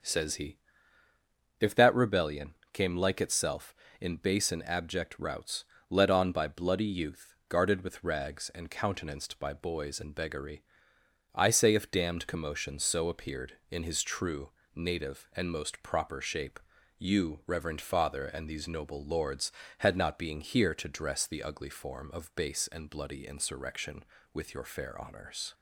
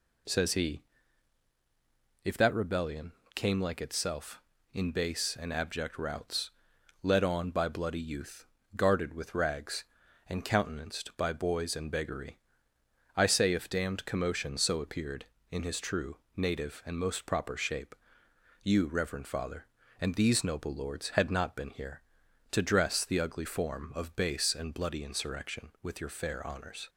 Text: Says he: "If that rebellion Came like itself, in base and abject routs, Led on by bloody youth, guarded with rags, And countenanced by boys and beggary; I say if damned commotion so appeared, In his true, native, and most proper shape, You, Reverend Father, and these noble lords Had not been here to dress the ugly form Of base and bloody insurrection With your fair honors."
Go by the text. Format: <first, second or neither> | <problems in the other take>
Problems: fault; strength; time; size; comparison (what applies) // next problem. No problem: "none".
second | starts louder than the rest; until 2.0 s; 6.5 dB // pauses between "rebellion" and "Came"; slight; at 2.5 s; 0.18 s long; slight in the second // says "being" for "been"; at 20.1 s